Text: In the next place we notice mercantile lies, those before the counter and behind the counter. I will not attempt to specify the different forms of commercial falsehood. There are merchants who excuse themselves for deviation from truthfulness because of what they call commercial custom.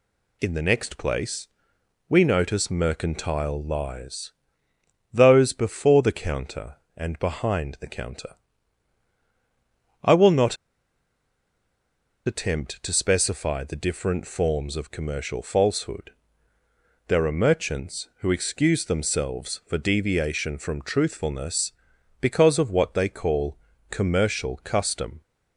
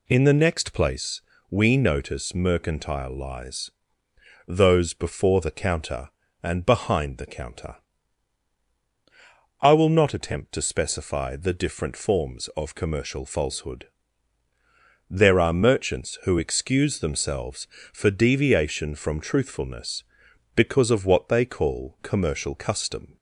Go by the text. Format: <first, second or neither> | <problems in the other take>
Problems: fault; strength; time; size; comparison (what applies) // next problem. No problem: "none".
second | pauses between "place" and "we"; noticeable; at 1.4 s; 0.60 s long; slight in the second // pauses between "not" and "attempt"; strong; at 10.5 s; 1.7 s long // pauses between "call" and "commercial"; slight; at 23.5 s; 0.34 s long